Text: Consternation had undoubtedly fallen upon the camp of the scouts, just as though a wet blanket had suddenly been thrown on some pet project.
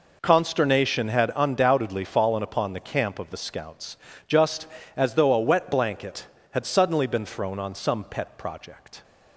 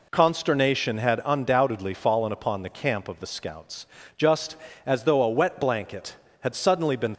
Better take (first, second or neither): first